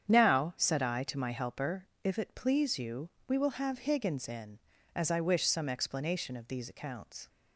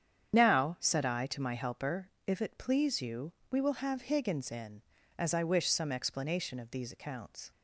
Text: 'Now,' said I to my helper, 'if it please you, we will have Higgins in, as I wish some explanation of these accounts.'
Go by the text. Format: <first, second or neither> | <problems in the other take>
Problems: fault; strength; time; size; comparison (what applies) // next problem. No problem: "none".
first | loses the start of "Now"; at 0.3 s; 25 ms // starts louder than the rest; strong; until 1.3 s; 8.5 dB; strong in the first